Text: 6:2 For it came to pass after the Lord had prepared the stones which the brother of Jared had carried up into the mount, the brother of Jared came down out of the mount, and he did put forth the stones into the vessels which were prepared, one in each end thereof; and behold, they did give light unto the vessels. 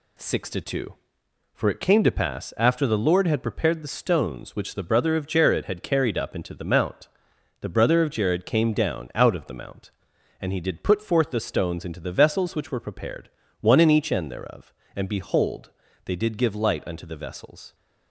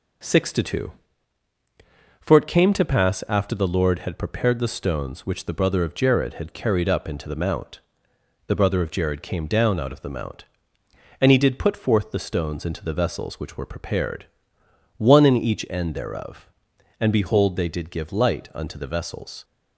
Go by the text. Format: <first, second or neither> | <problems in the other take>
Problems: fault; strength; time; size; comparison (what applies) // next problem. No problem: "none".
neither | none